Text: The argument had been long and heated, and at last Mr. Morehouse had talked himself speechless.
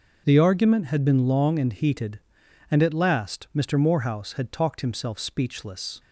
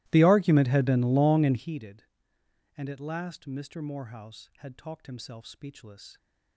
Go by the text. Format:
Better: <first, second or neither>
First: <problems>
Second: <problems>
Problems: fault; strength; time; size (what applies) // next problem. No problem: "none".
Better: first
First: none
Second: starts louder than the rest; strong; until 1.7 s; 19 dB